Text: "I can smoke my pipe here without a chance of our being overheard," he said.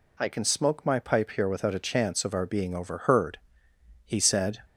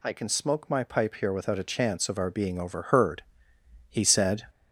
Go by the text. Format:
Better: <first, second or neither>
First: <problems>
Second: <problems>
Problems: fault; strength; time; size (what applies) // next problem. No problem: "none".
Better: first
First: none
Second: gets louder; noticeable; throughout; 4.5 dB